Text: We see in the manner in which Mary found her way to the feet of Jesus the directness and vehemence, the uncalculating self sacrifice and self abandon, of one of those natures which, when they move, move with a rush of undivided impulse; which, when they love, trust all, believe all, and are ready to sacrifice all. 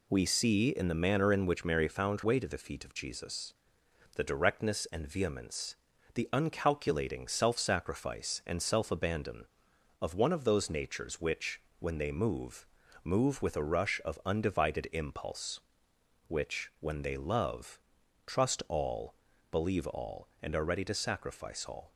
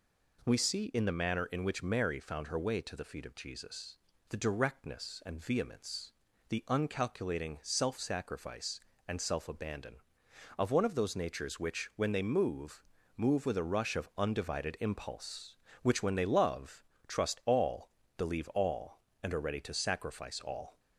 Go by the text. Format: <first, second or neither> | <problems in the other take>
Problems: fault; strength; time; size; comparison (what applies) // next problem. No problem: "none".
second | skips "her"; at 2.2 s // pauses between "Jesus" and "the"; noticeable; at 3.5 s; 0.62 s long; slight in the second